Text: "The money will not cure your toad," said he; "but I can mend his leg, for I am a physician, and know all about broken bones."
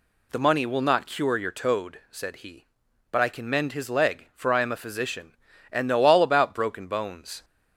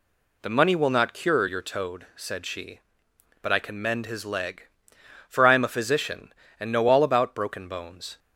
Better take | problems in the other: first | says "she" for "he"; at 2.4 s

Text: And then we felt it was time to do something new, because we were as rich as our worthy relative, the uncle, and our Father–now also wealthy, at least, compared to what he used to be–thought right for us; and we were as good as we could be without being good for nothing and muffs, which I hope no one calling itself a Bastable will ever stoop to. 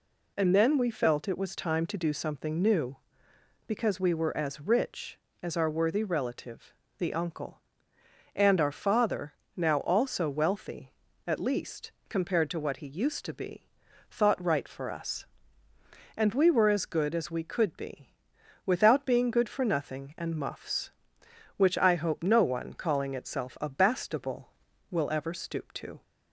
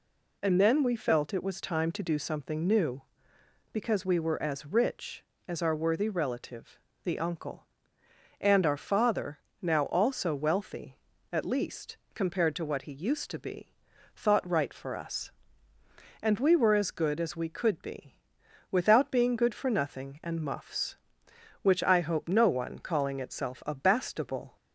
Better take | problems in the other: first | pauses between "be" and "without"; noticeable; at 18.1 s; 0.56 s long; noticeable in the first // stops before "will ever stoop to"; at 24.5 s

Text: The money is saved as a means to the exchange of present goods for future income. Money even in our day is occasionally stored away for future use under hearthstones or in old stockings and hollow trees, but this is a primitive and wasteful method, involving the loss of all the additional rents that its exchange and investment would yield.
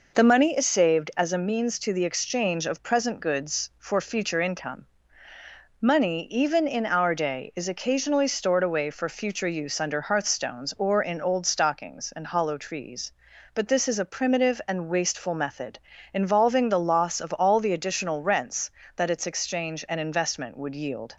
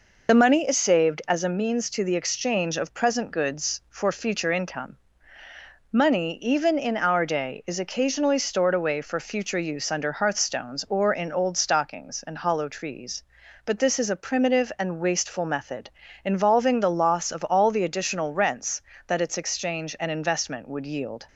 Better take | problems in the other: first | loses the start of "The"; at 0.2 s; 40 ms

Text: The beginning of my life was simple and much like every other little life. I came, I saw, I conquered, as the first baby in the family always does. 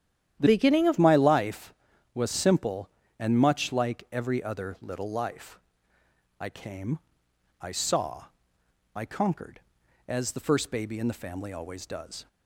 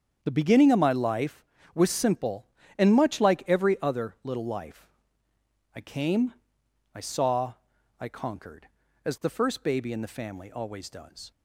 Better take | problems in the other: second | starts louder than the rest; strong; until 1.4 s; 10.5 dB; strong in the second // changes voice from "beginning" to "of"; from 0.4 to 0.9 s; 0.5 s long

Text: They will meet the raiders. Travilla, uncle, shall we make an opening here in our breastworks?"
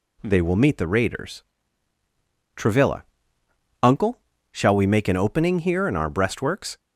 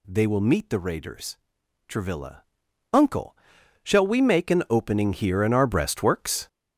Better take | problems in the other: first | gets louder; strong; throughout; 8 dB

